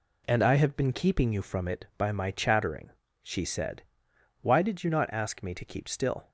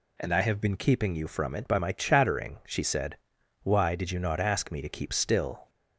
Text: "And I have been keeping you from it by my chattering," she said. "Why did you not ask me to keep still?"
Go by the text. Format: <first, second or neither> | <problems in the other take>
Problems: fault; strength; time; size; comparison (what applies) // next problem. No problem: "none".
neither | none